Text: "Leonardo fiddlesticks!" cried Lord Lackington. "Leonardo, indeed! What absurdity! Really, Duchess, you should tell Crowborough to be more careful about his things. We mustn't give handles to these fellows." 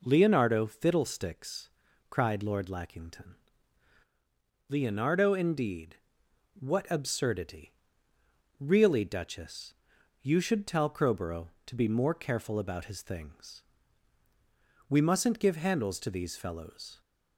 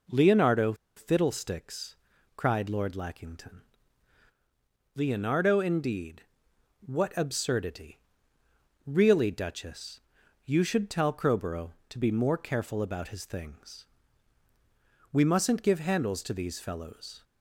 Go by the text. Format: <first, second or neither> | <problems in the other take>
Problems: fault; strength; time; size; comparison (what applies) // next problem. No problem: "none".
first | pauses between "Leonardo" and "fiddlesticks"; slight; at 0.7 s; 0.22 s long